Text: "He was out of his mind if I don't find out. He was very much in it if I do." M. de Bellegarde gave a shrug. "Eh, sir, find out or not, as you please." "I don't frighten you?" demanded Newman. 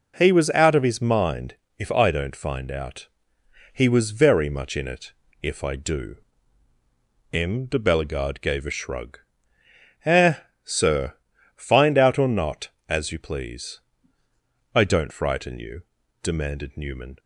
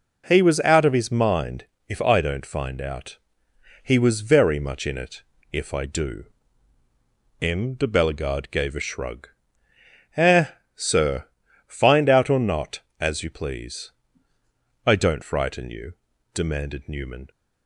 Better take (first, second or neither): neither